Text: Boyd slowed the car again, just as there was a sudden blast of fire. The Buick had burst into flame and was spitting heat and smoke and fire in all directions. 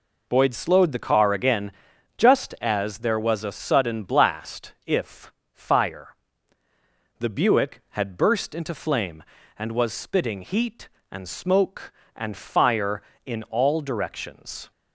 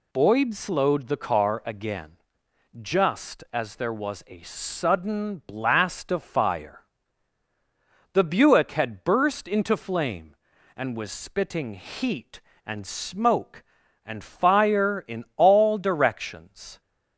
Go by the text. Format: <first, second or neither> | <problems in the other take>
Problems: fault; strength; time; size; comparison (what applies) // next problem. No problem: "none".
second | says "if" for "of"; at 4.8 s